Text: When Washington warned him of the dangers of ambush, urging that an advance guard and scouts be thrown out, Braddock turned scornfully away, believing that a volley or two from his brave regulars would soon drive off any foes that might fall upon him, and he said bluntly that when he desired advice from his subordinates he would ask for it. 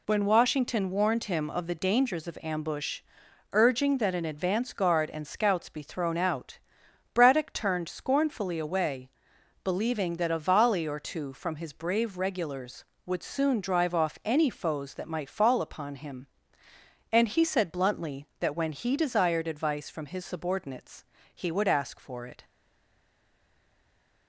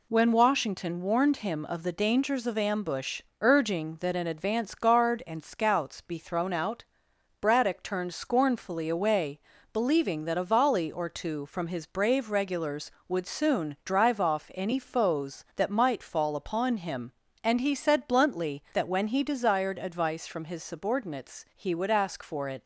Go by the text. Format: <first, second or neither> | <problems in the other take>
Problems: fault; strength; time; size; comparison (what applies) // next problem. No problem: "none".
second | pauses between "subordinates" and "he"; slight; at 21.0 s; 0.30 s long // stays silent after the last word; noticeable; from 22.4 s on; 1.8 s long